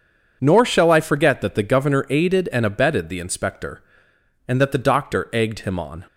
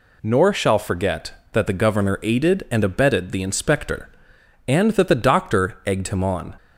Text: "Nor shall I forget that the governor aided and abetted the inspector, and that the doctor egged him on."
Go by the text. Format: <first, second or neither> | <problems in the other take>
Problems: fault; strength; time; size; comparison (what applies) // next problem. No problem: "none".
first | skips "I"; at 0.7 s